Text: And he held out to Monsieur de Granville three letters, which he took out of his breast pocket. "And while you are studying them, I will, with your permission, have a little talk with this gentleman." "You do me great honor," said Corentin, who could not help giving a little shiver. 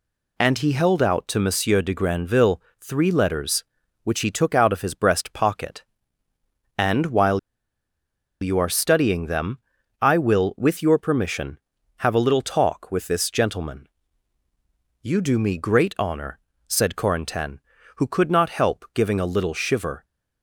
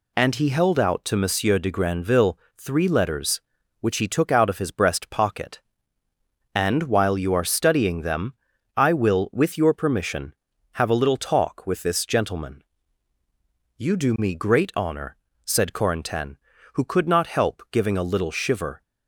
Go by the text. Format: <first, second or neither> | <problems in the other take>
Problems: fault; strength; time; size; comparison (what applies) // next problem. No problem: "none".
second | pauses between "Granville" and "three"; slight; at 2.6 s; 0.20 s long; slight in the second // pauses between "while" and "you"; at 7.3 s; 1.0 s long